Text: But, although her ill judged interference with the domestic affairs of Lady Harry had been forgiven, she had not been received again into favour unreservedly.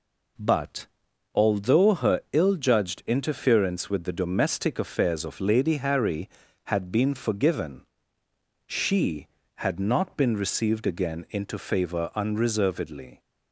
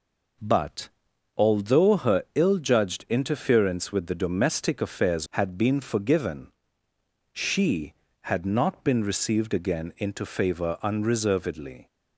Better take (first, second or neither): first